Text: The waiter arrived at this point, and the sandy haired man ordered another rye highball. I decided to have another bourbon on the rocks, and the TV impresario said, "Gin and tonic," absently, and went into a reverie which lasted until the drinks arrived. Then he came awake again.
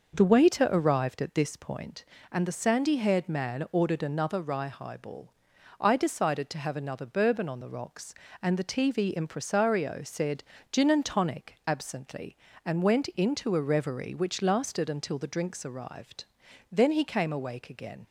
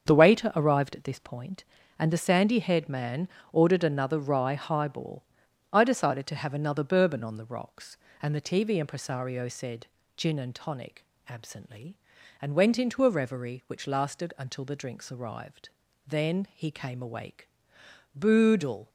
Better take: first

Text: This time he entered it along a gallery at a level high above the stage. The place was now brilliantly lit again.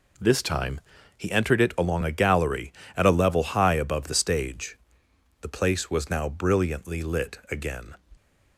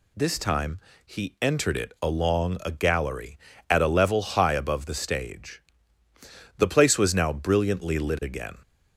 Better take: neither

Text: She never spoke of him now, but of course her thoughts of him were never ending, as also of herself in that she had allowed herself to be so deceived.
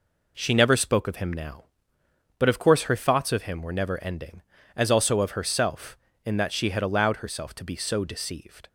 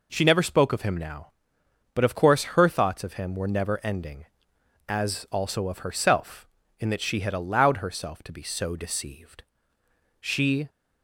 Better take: first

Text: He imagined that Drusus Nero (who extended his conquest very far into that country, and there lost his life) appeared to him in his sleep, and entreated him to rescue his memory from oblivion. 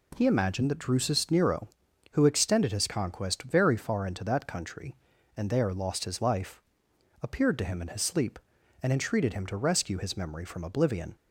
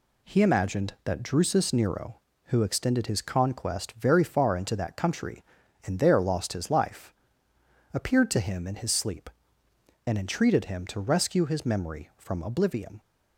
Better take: neither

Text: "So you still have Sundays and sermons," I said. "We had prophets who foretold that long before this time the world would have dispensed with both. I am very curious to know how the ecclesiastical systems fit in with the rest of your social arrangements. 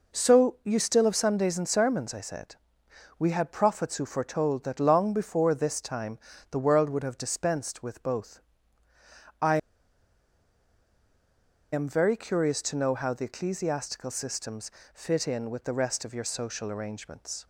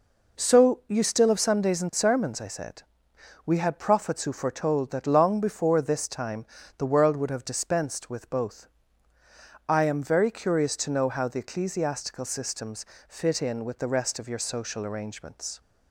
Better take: second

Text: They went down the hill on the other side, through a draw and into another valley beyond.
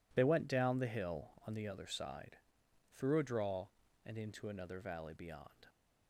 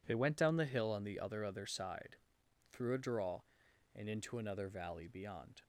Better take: first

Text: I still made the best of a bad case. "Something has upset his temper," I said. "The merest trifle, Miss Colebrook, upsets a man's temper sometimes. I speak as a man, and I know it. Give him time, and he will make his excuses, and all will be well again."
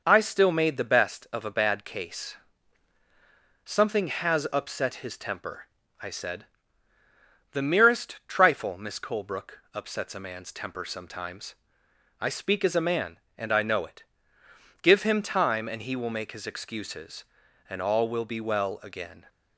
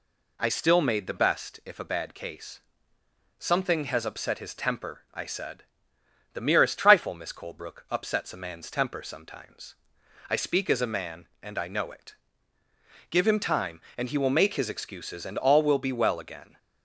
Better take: first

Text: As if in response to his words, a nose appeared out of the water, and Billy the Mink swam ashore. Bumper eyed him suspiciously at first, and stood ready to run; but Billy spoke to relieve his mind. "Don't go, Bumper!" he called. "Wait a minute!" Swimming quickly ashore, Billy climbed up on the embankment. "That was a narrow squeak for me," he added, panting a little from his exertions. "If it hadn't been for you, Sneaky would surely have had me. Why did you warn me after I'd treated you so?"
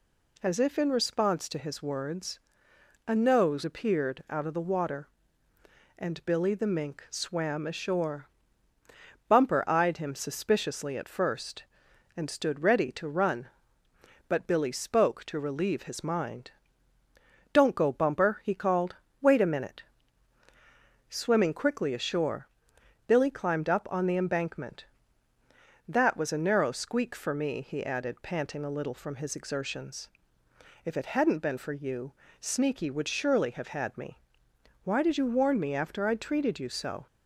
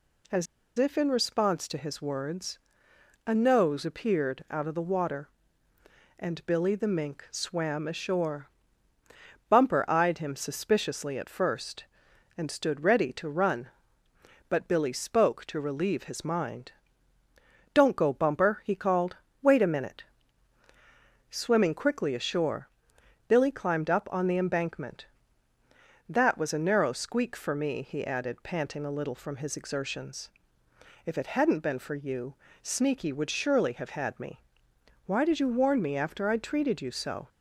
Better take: first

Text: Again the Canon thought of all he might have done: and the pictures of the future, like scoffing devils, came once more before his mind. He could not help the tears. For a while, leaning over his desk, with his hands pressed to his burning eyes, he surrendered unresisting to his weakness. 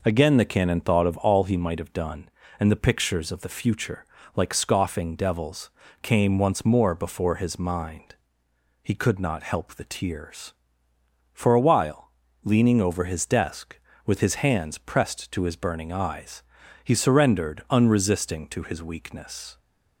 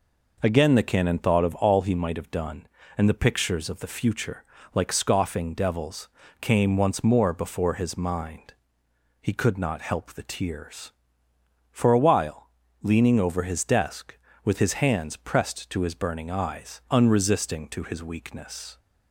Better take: first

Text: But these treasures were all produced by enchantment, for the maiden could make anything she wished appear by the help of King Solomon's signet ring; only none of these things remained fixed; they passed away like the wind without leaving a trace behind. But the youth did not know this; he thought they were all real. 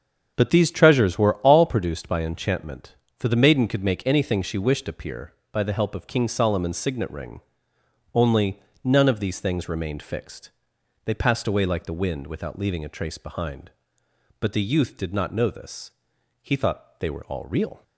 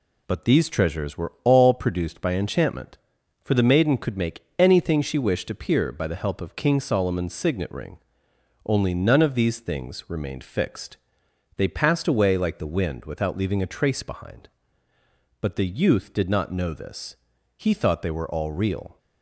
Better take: second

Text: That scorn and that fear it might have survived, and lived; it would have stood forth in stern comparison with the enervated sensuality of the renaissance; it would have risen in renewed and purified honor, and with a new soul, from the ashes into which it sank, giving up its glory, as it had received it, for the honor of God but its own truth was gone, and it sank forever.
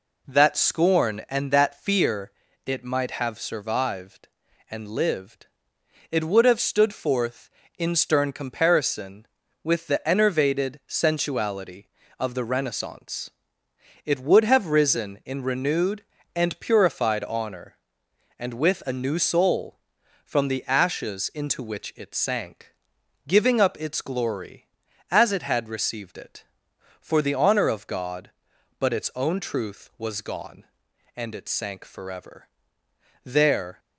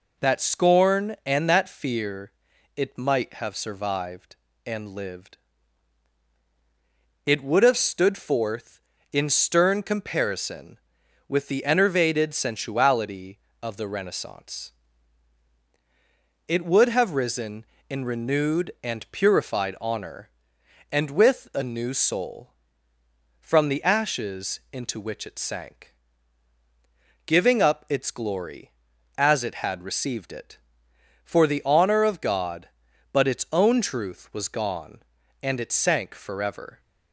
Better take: second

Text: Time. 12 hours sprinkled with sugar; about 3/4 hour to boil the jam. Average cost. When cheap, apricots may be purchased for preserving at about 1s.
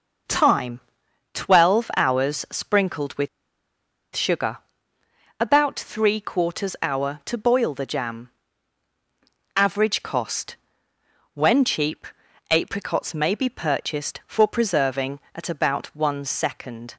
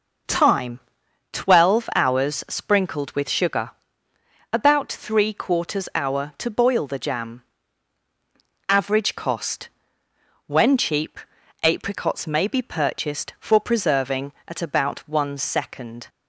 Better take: second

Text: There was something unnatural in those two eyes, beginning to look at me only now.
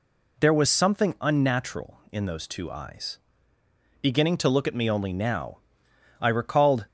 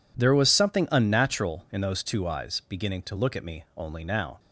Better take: second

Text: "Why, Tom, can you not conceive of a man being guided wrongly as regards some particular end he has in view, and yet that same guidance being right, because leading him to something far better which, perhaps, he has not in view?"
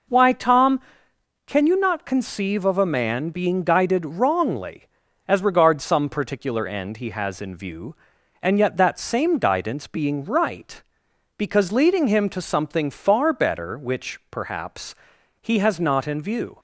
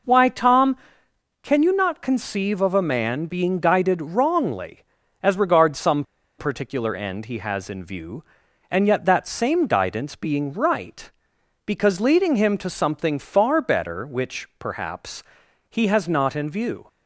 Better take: first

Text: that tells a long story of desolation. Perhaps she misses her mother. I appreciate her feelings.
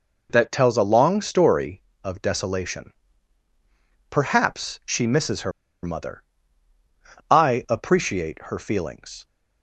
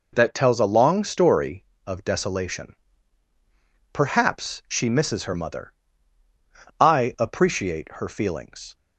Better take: second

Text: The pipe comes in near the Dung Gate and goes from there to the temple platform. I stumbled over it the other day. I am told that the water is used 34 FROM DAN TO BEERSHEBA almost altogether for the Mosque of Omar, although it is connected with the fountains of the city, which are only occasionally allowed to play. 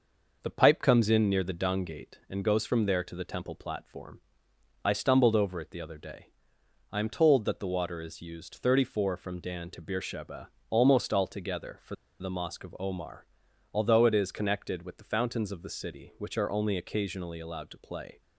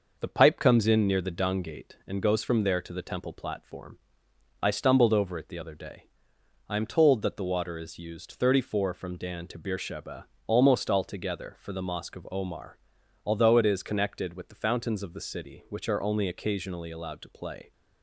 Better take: second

